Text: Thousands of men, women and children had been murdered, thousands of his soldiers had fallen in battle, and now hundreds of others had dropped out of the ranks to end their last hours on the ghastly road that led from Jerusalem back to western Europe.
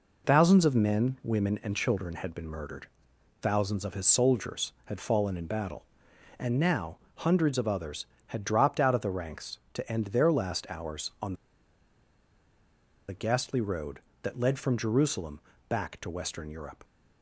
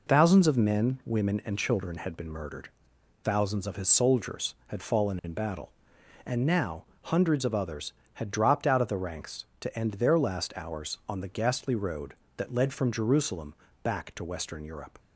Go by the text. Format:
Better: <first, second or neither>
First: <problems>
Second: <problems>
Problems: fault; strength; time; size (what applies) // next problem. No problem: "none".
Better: second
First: pauses between "now" and "hundreds"; slight; at 6.9 s; 0.20 s long // pauses between "on" and "the"; strong; at 11.3 s; 1.7 s long // pauses between "Jerusalem" and "back"; slight; at 15.3 s; 0.28 s long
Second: pauses between "now" and "hundreds"; slight; at 6.8 s; 0.20 s long // pauses between "Jerusalem" and "back"; slight; at 13.5 s; 0.28 s long